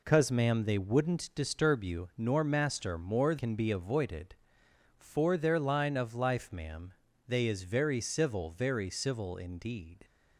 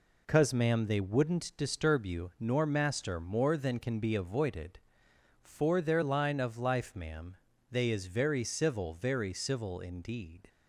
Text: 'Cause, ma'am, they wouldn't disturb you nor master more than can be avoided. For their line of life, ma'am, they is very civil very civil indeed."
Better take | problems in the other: second | skips "than"; at 3.3 s

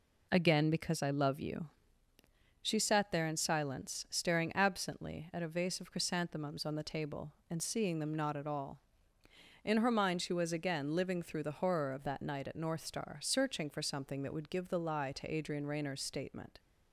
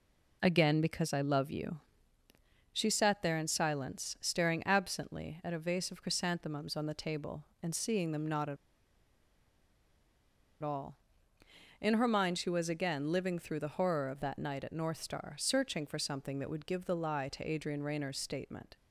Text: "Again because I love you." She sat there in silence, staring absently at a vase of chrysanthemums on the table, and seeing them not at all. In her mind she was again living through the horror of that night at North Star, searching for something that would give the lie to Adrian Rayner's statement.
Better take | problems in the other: first | pauses between "at" and "all"; strong; at 8.5 s; 2.0 s long

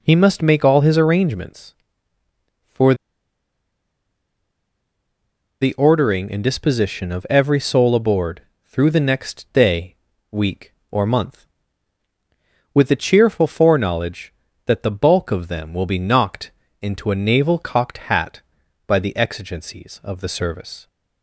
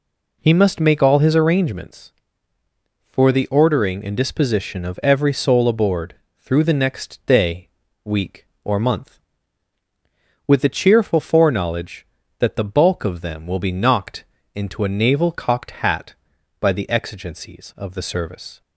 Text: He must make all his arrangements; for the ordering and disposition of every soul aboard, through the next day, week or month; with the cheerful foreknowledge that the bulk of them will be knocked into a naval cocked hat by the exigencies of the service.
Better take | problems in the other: second | pauses between "for" and "the"; strong; at 2.9 s; 2.6 s long // pauses between "knocked" and "into"; slight; at 16.4 s; 0.32 s long; slight in the second

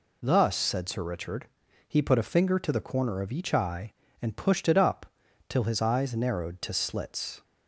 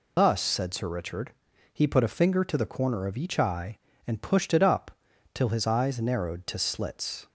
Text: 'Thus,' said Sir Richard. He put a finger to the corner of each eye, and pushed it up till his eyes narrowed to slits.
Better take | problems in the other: first | loses the start of "Thus"; at 0.1 s; 95 ms // pauses between "up" and "till"; at 4.8 s; 0.42 s long; also in the first

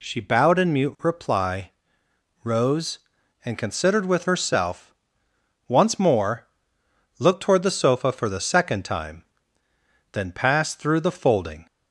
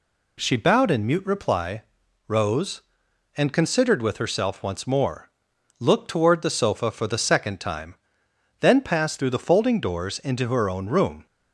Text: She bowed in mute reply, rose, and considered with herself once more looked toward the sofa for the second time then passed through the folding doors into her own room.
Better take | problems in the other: second | pauses between "herself" and "once"; noticeable; at 4.9 s; 0.74 s long // pauses between "more" and "looked"; noticeable; at 6.4 s; 0.72 s long; noticeable in the second // pauses between "time" and "then"; noticeable; at 9.2 s; 0.88 s long; noticeable in the second // stops before "doors into her own room"; at 11.6 s

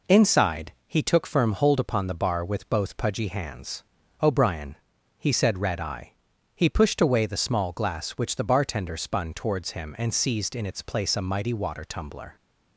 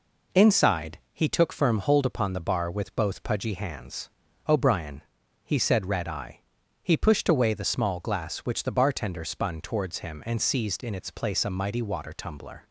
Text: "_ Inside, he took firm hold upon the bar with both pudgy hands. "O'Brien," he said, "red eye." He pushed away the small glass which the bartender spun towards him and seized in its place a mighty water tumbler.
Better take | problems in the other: neither | none

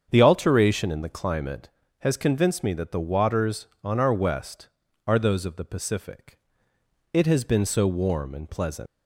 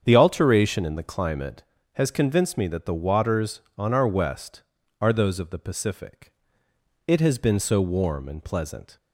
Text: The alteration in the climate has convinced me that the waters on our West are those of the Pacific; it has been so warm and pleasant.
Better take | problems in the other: second | starts louder than the rest; strong; until 1.1 s; 7.5 dB; strong in the second // leaves "pleasant" unfinished; at 8.8 s; 160 ms

